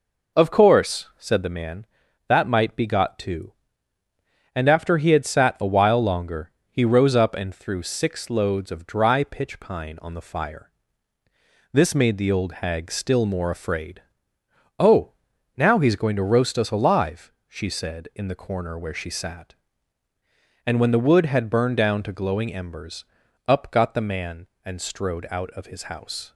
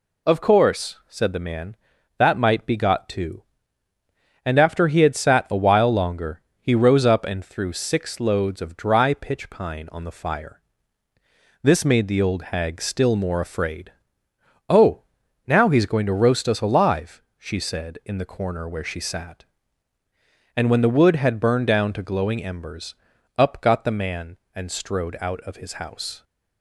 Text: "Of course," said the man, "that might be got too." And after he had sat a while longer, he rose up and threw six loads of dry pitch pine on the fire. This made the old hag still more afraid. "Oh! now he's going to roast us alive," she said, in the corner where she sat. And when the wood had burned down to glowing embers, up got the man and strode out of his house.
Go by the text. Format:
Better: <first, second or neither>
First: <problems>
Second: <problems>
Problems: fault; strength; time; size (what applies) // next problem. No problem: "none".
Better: second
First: starts louder than the rest; noticeable; until 1.6 s; 4.5 dB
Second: none